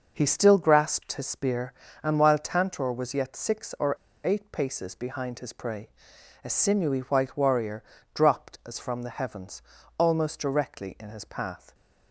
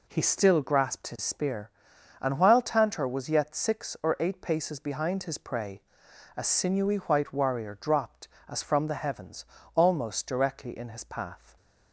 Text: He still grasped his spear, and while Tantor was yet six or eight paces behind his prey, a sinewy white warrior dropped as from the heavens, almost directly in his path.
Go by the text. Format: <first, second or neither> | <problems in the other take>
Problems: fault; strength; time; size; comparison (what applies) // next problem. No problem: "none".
second | pauses between "or" and "eight"; slight; at 3.9 s; 0.30 s long // pauses between "warrior" and "dropped"; slight; at 7.8 s; 0.28 s long